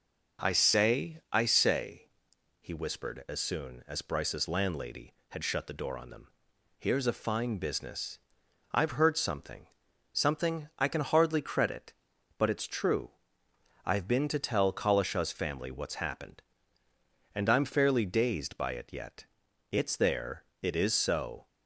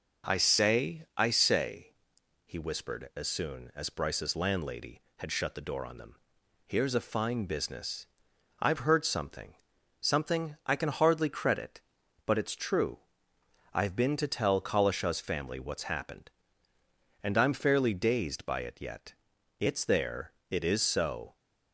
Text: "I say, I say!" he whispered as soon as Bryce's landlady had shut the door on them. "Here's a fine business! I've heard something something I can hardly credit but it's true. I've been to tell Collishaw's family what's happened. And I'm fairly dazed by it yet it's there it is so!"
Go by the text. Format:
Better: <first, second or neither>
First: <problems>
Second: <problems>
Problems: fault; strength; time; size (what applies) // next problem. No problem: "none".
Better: neither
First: pauses between "something" and "something"; noticeable; at 9.6 s; 0.48 s long // pauses between "yet" and "it's"; noticeable; at 19.2 s; 0.46 s long // pauses between "there" and "it"; slight; at 20.4 s; 0.16 s long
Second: pauses between "something" and "something"; noticeable; at 9.5 s; 0.48 s long // pauses between "yet" and "it's"; noticeable; at 19.1 s; 0.46 s long // pauses between "there" and "it"; slight; at 20.3 s; 0.16 s long